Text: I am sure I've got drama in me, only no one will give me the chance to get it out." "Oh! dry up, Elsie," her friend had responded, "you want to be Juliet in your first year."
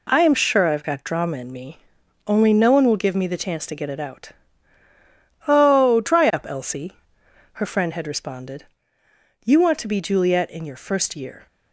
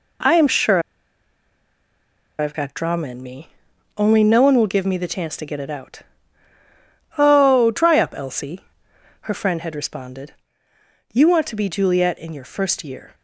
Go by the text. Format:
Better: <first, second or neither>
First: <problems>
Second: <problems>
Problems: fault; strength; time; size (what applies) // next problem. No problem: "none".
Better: first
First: none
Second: pauses between "sure" and "I've"; strong; at 0.7 s; 1.5 s long